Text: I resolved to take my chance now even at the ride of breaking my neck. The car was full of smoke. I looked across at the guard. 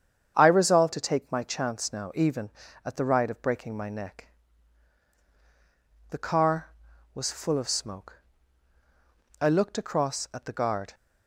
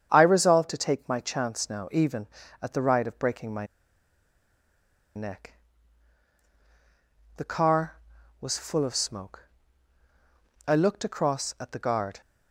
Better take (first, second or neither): first